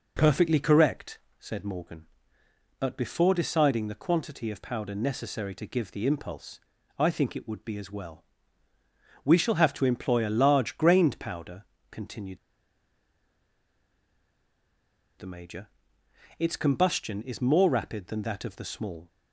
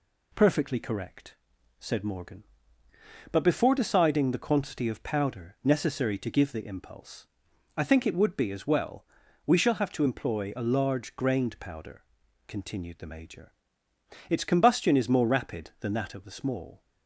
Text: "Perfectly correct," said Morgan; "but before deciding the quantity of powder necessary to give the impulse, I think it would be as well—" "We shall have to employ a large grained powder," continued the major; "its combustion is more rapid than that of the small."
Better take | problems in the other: second | pauses between "continued" and "the"; strong; at 12.3 s; 2.8 s long

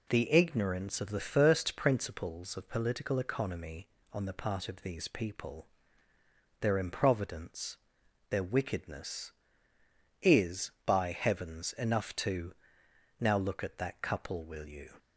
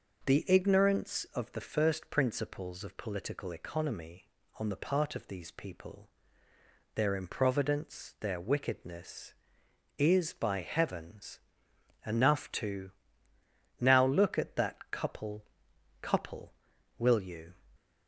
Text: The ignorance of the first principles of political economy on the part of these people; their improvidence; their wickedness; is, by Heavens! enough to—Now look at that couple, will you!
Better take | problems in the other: first | says "couple" twice; at 16.0 s

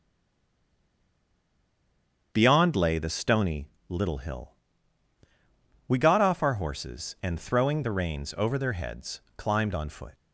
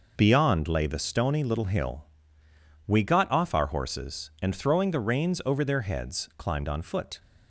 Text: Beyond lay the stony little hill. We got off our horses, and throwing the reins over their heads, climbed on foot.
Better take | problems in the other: second | stays silent before the first word; until 2.3 s; 2.3 s long // starts louder than the rest; strong; until 3.3 s; 7.5 dB // pauses between "stony" and "little"; slight; at 3.6 s; 0.22 s long

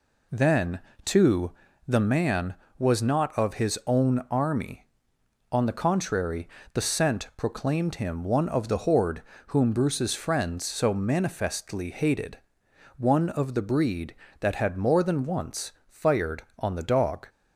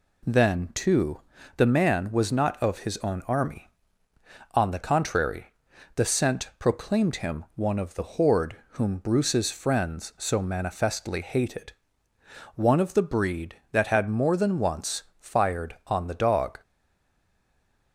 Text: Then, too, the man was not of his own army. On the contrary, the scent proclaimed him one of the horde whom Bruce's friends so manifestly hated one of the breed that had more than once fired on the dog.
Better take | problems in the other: first | pauses between "horde" and "whom"; slight; at 8.5 s; 0.16 s long; slight in the first // pauses between "hated" and "one"; noticeable; at 11.7 s; 0.84 s long; noticeable in the first // pauses between "once" and "fired"; slight; at 15.0 s; 0.16 s long; slight in the first // stays silent after the last word; noticeable; from 16.6 s on; 1.3 s long

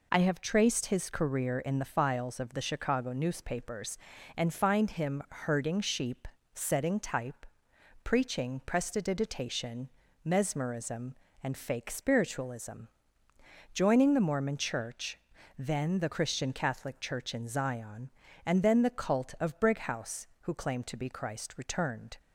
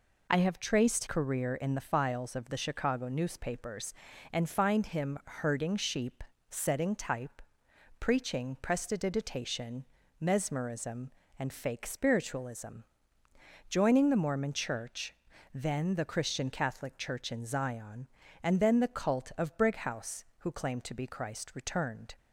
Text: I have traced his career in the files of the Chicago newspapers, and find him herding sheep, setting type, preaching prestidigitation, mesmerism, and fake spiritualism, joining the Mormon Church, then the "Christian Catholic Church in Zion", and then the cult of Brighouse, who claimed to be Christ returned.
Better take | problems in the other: first | skips "his"; at 1.0 s

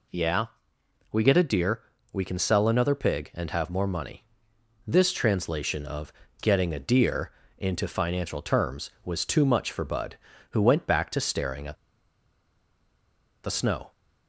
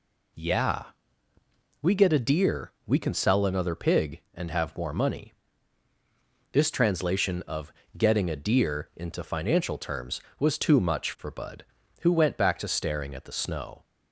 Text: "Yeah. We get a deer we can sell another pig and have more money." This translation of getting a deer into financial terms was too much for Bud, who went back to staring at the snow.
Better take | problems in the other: second | pauses between "deer" and "we"; slight; at 1.8 s; 0.32 s long // pauses between "of" and "getting"; slight; at 6.1 s; 0.26 s long; slight in the second // pauses between "deer" and "into"; slight; at 7.3 s; 0.28 s long // pauses between "at" and "the"; strong; at 11.7 s; 1.6 s long

